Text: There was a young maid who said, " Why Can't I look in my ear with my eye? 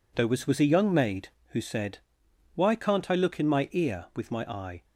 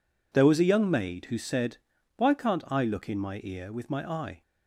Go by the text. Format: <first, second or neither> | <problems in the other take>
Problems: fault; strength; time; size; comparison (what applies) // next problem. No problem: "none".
second | says "was" twice; at 0.4 s